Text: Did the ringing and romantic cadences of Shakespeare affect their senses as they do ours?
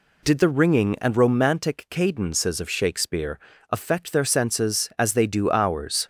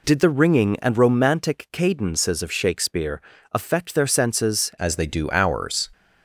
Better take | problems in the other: first | pauses between "Shakespeare" and "affect"; slight; at 3.2 s; 0.30 s long; slight in the first // changes voice at "as"; from 4.7 s on; 1.1 s long

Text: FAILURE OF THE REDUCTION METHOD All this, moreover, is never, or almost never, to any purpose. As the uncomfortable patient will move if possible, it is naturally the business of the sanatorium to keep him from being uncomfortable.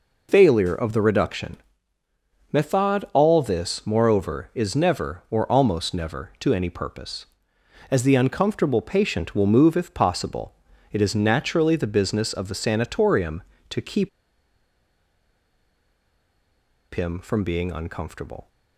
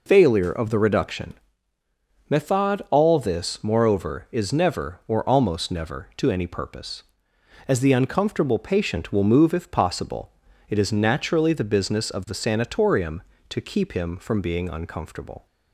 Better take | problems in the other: second | pauses between "REDUCTION" and "METHOD"; noticeable; at 1.5 s; 0.96 s long; noticeable in the second // pauses between "keep" and "him"; strong; at 14.0 s; 2.8 s long

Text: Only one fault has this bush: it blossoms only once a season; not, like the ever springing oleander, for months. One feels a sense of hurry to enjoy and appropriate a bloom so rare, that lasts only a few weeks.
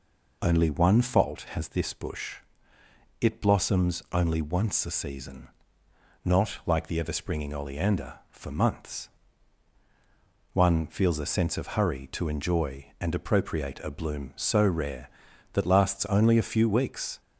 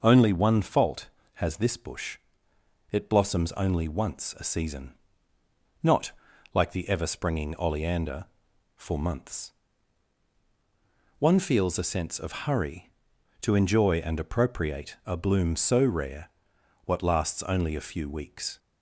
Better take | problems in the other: first | says "what" for "that"; at 16.8 s

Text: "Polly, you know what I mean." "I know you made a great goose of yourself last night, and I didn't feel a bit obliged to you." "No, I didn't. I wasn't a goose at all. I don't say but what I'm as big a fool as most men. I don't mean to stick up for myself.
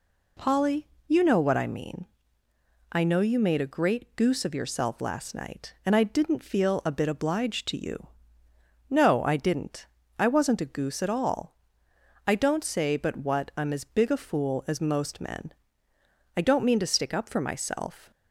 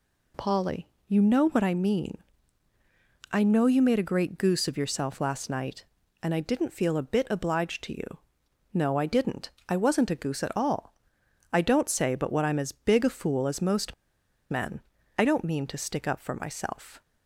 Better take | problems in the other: first | pauses between "most" and "men"; noticeable; at 13.9 s; 0.57 s long

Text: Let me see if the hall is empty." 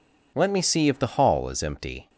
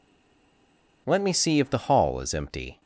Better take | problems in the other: first | stays silent before the first word; until 1.0 s; 1.0 s long

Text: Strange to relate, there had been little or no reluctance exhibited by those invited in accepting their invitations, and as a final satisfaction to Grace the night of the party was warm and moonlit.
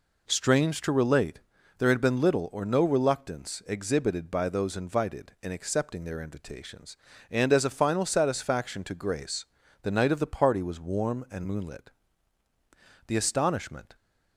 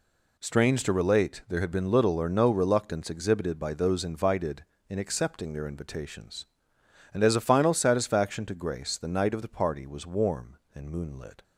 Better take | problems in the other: second | pauses between "Grace" and "the"; at 9.4 s; 0.38 s long // goes on to say "The astonishment"; noticeable; from 13.0 s on; 0.88 s long

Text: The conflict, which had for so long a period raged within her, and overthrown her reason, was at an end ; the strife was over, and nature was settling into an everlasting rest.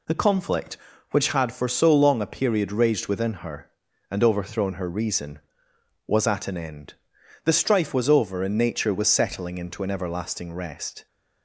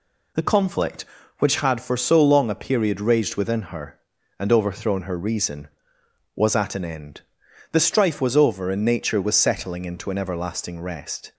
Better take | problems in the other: neither | none

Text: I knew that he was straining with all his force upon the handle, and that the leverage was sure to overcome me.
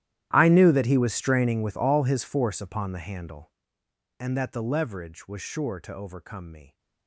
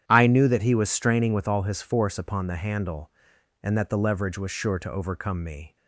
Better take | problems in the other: second | gets quieter; strong; throughout; 22.5 dB // starts louder than the rest; strong; until 1.3 s; 12.5 dB; strong in the second

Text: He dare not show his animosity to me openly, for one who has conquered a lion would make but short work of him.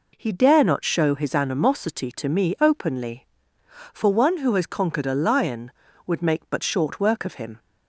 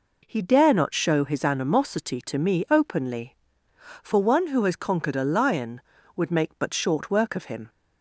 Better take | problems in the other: neither | none

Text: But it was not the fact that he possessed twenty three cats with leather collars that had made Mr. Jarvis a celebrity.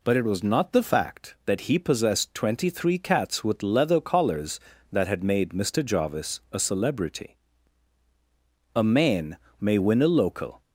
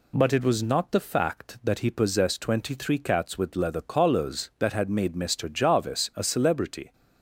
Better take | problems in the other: second | goes on to say "A man may win a local"; strong; from 8.7 s on; 1.8 s long

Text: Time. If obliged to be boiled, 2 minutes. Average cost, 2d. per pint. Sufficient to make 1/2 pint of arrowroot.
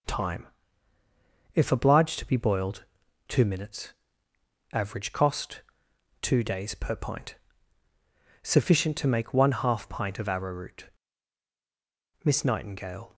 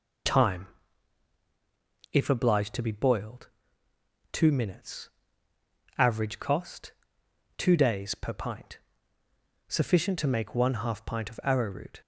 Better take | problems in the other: second | goes on to say "MISS NIGHTINGALE"; noticeable; from 12.2 s on; 0.92 s long

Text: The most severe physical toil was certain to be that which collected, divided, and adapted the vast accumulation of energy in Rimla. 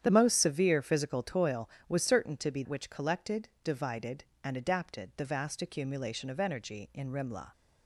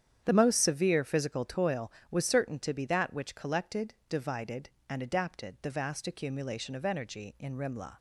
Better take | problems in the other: second | starts louder than the rest; strong; until 1.0 s; 9.5 dB; strong in the second // skips "that"; at 2.6 s

